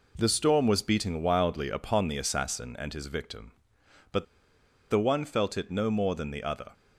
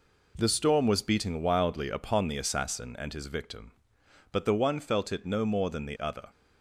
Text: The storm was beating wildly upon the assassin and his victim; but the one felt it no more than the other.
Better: second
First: pauses between "but" and "the"; noticeable; at 4.2 s; 0.66 s long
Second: none

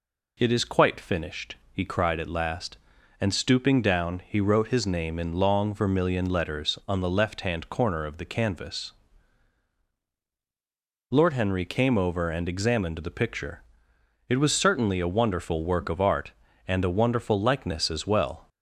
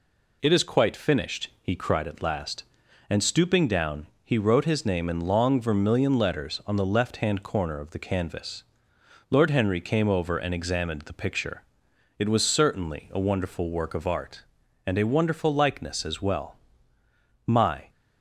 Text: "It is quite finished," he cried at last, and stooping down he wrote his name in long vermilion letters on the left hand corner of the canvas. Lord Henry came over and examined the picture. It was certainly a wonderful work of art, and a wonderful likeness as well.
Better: first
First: none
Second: pauses between "down" and "he"; slight; at 4.0 s; 0.18 s long // goes on to say "My"; slight; from 17.4 s on; 0.44 s long

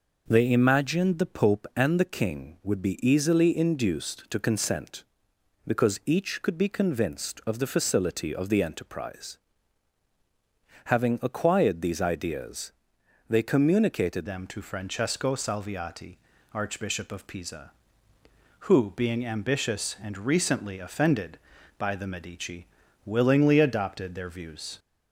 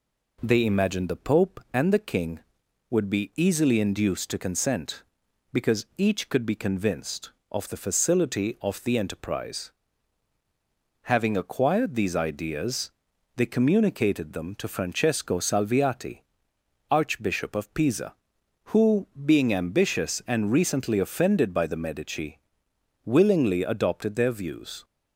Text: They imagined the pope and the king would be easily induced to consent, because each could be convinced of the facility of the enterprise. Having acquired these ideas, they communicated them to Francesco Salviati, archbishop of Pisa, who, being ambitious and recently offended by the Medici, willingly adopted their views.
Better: second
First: changes voice at "them"; from 14.2 s on; 10.5 s long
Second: none

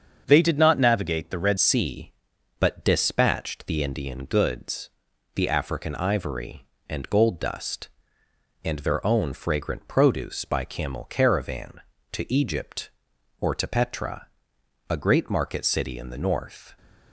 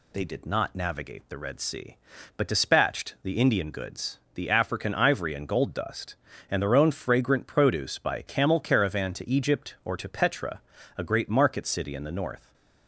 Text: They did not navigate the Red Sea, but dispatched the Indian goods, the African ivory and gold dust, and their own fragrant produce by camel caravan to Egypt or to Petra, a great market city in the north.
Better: second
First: starts louder than the rest; until 1.2 s; 7 dB // changes voice at "Sea"; from 1.5 s on; 15.2 s long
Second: none

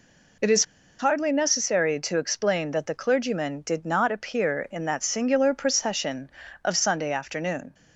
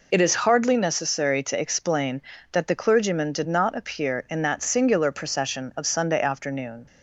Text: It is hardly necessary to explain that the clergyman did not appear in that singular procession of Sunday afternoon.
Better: second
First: pauses between "is" and "hardly"; at 0.6 s; 0.36 s long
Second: none

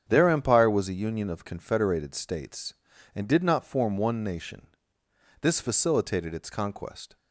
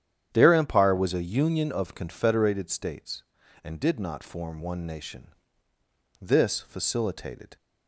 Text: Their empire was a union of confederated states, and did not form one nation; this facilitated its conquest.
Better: first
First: starts louder than the rest; strong; until 1.1 s; 8 dB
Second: starts louder than the rest; strong; until 1.3 s; 9.5 dB // stops before "its conquest"; at 7.5 s

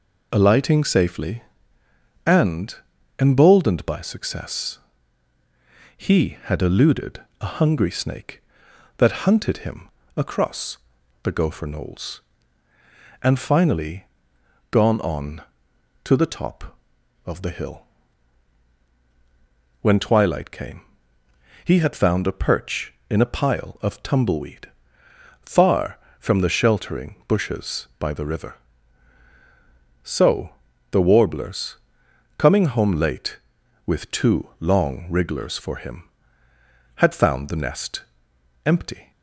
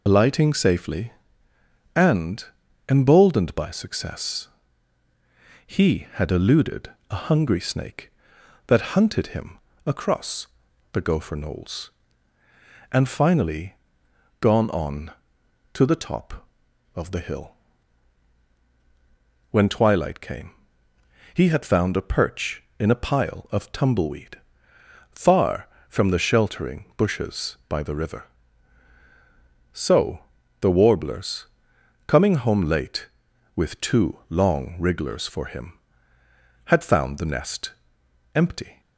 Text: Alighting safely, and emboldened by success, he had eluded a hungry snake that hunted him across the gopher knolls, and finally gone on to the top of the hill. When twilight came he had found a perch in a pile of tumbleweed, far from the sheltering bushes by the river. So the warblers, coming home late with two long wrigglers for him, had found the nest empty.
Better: first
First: pauses between "and" and "emboldened"; at 2.7 s; 0.42 s long // pauses between "eluded" and "a"; slight; at 7.2 s; 0.20 s long // pauses between "him" and "across"; slight; at 9.8 s; 0.28 s long // pauses between "across" and "the"; at 10.7 s; 0.44 s long // pauses between "finally" and "gone"; noticeable; at 14.0 s; 0.70 s long // pauses between "came" and "he"; noticeable; at 20.8 s; 0.82 s long // pauses between "So" and "the"; at 30.5 s; 0.42 s long // pauses between "nest" and "empty"; noticeable; at 38.0 s; 0.62 s long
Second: loses the start of "Alighting"; at 0.0 s; 40 ms // pauses between "and" and "emboldened"; at 2.4 s; 0.42 s long // pauses between "eluded" and "a"; slight; at 6.9 s; 0.20 s long // pauses between "him" and "across"; slight; at 9.5 s; 0.28 s long // pauses between "across" and "the"; at 10.4 s; 0.44 s long // pauses between "finally" and "gone"; noticeable; at 13.7 s; 0.70 s long // pauses between "came" and "he"; noticeable; at 20.5 s; 0.82 s long // pauses between "So" and "the"; at 30.2 s; 0.42 s long // pauses between "nest" and "empty"; noticeable; at 37.7 s; 0.62 s long

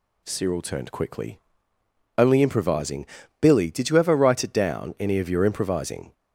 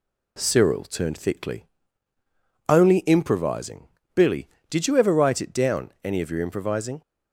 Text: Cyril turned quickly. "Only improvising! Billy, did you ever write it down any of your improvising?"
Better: first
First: none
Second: says "thickly" for "quickly"; at 1.1 s

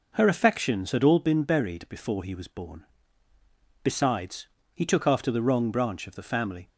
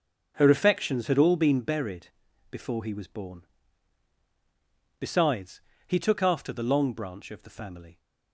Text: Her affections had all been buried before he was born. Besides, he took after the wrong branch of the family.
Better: first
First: none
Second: starts louder than the rest; until 1.3 s; 7 dB // pauses between "buried" and "before"; at 2.0 s; 0.44 s long // says "long" for "wrong"; at 6.6 s

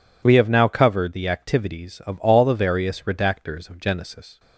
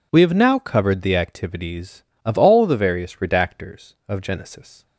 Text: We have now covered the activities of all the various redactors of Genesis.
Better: neither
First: none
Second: none

